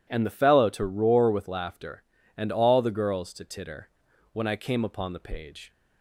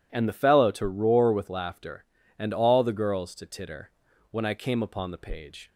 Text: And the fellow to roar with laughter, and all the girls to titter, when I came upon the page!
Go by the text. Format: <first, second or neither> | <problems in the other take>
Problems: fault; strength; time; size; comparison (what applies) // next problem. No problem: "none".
neither | none